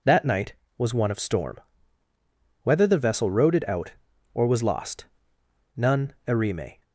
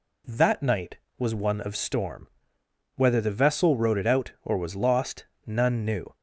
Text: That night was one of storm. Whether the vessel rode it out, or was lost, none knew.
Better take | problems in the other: second | says "erime" for "knew"; at 6.2 s

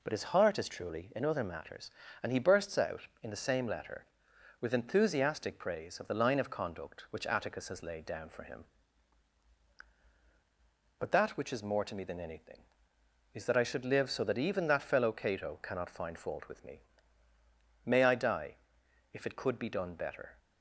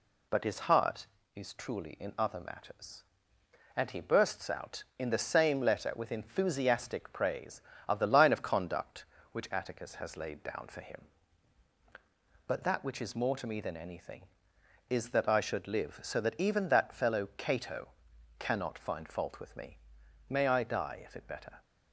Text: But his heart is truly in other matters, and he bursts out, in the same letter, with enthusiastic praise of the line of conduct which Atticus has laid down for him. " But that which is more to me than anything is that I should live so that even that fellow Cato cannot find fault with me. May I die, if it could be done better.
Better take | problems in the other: first | pauses between "Cato" and "cannot"; noticeable; at 17.9 s; 0.48 s long // skips "could be done"; at 21.2 s

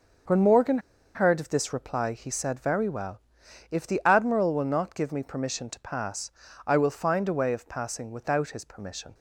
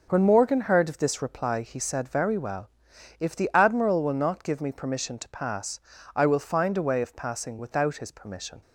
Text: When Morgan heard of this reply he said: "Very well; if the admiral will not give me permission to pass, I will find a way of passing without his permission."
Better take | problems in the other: second | starts louder than the rest; noticeable; until 1.6 s; 6 dB // pauses between "Morgan" and "heard"; at 0.7 s; 0.36 s long

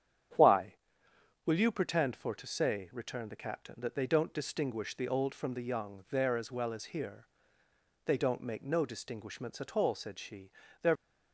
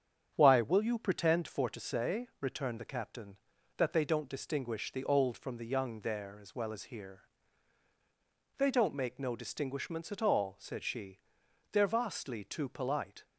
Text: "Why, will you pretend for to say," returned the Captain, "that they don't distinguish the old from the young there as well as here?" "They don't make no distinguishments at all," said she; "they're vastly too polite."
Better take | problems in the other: second | starts louder than the rest; strong; until 2.0 s; 9 dB; strong in the second // stops before "vastly too polite"; at 10.9 s

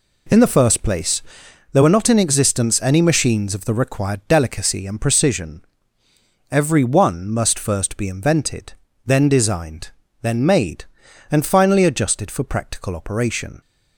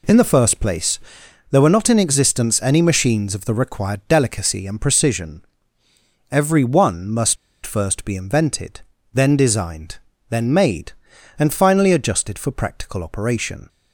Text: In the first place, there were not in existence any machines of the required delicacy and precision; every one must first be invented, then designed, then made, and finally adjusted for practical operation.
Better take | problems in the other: first | pauses between "must" and "first"; slight; at 7.3 s; 0.30 s long

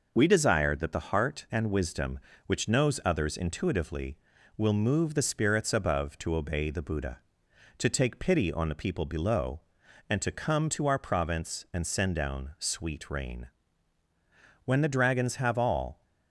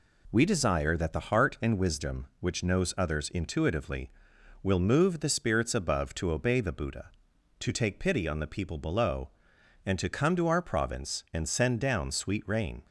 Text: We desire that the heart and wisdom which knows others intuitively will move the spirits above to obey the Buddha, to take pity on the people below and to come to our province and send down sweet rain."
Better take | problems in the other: second | goes on to say "When the dragons have all"; from 14.6 s on; 1.3 s long

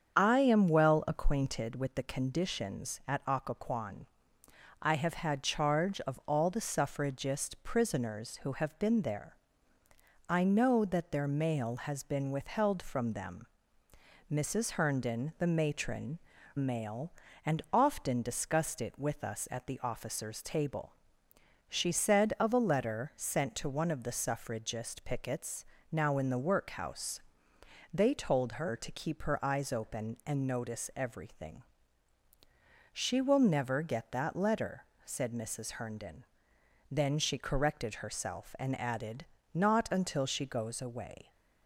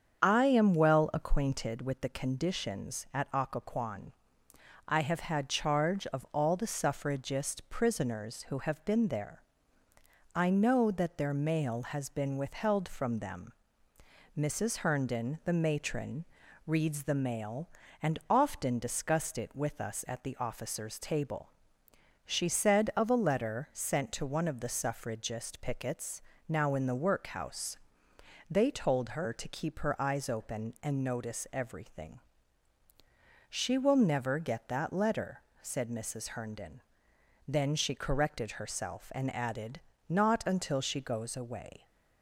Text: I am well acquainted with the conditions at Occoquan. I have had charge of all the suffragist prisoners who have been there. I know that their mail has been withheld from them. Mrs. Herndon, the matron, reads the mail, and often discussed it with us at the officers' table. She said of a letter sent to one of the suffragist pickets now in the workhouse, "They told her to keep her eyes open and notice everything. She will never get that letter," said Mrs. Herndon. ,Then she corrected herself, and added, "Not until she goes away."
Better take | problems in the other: second | starts louder than the rest; strong; until 1.1 s; 7.5 dB; strong in the second // skips "reads the"; at 16.3 s // pauses between "pickets" and "now"; slight; at 25.6 s; 0.26 s long; slight in the second

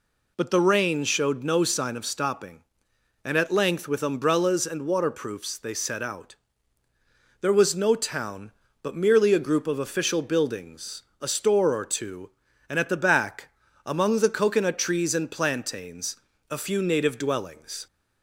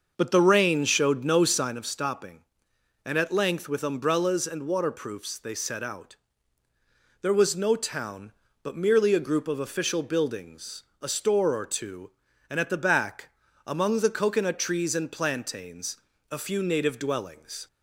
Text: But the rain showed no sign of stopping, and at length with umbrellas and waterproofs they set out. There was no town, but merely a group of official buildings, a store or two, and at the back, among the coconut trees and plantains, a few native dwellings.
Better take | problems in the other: first | starts louder than the rest; noticeable; until 1.7 s; 6 dB

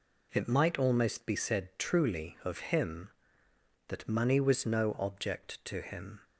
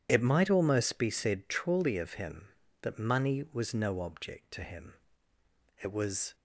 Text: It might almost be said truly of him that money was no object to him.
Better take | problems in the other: first | goes on to say "It was"; from 5.8 s on; 0.54 s long

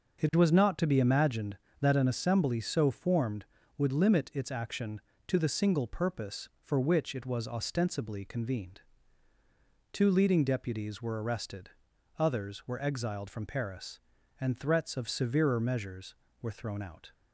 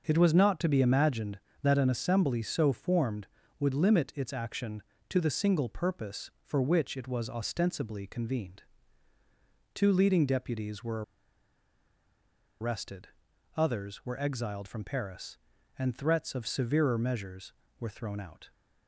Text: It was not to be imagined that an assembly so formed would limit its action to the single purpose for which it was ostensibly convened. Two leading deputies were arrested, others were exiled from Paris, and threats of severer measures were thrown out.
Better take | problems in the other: first | starts louder than the rest; until 1.0 s; 6 dB; also in the first // pauses between "were" and "arrested"; strong; at 11.0 s; 1.5 s long

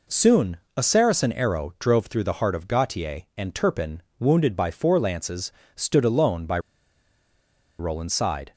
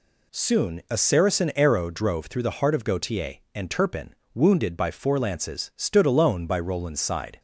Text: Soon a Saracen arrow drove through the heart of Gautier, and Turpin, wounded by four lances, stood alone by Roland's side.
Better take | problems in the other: second | pauses between "Soon" and "a"; slight; at 0.5 s; 0.18 s long // pauses between "by" and "Roland's"; at 6.5 s; 1.2 s long

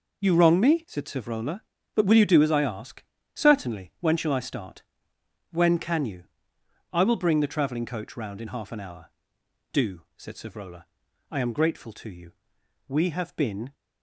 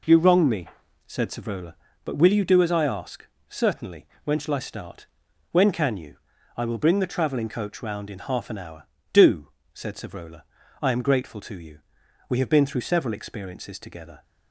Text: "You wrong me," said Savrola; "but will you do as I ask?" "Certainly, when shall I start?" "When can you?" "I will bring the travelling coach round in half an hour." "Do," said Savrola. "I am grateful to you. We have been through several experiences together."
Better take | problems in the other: second | stops before "through several experiences together"; at 13.7 s

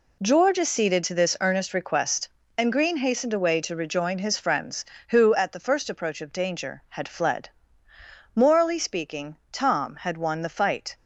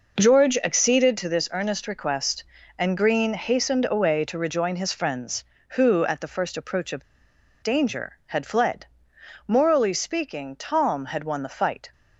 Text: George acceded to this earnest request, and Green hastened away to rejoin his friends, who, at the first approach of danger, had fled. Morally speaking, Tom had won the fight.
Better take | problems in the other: first | pauses between "of" and "danger"; noticeable; at 7.0 s; 0.58 s long

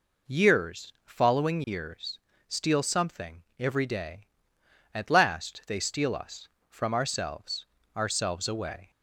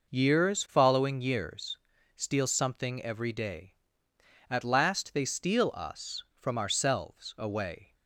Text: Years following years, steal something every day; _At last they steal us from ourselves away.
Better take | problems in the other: second | says "ourselves" twice; at 7.9 s

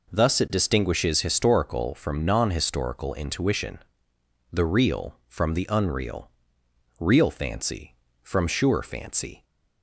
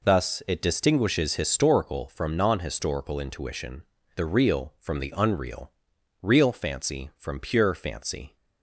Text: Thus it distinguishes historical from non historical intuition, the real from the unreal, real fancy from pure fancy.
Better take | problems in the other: second | says "sure" for "pure"; at 8.4 s

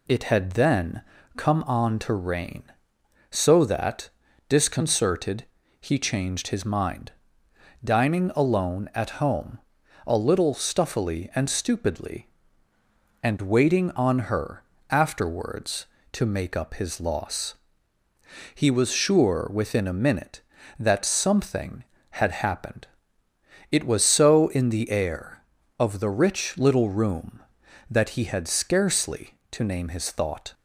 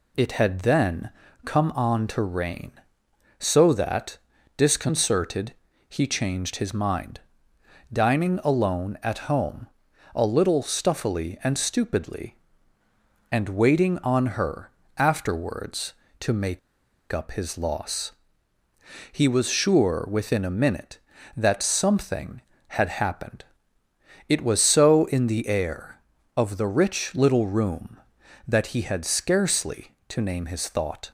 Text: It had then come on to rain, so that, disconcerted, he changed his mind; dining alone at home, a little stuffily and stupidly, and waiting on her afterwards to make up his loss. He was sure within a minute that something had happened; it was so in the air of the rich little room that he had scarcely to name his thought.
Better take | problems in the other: first | pauses between "then" and "come"; slight; at 1.1 s; 0.34 s long; slight in the first // pauses between "her" and "afterwards"; slight; at 14.7 s; 0.26 s long; slight in the first // pauses between "make" and "up"; noticeable; at 16.5 s; 0.52 s long

